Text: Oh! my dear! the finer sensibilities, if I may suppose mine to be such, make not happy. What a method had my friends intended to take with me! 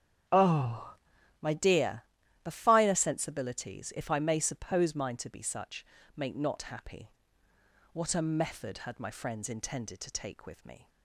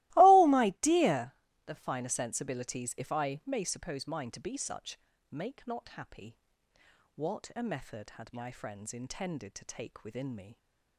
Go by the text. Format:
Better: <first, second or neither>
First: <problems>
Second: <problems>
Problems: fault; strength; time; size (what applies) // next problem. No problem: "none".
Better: first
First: starts louder than the rest; strong; until 1.7 s; 8 dB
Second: starts louder than the rest; strong; until 1.2 s; 19 dB // says "within" for "with"; at 10.0 s